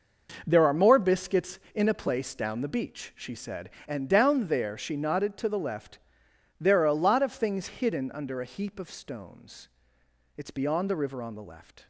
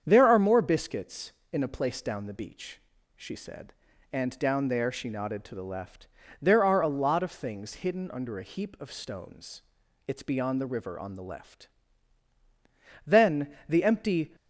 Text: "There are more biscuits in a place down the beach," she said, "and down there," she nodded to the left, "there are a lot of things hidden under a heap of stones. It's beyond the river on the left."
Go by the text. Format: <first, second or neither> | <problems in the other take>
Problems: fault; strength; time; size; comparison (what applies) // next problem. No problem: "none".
first | starts louder than the rest; strong; until 1.0 s; 7.5 dB // goes on to say "Then the empty"; noticeable; from 13.0 s on; 1.3 s long